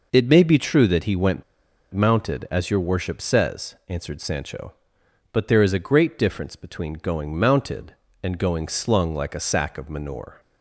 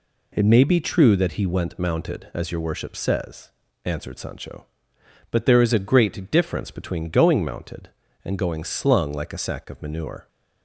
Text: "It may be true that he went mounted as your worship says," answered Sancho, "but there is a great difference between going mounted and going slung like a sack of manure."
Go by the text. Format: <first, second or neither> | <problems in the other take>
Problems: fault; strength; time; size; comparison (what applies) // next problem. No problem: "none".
second | pauses between "went" and "mounted"; noticeable; at 1.4 s; 0.50 s long